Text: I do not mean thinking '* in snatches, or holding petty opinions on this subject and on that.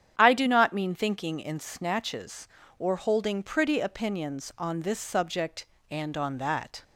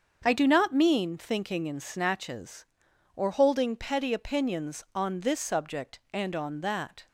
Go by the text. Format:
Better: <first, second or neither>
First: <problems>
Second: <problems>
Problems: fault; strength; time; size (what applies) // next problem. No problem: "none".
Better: second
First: starts louder than the rest; strong; until 1.1 s; 9 dB // says "pretty" for "petty"; at 3.4 s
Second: starts louder than the rest; until 1.2 s; 7 dB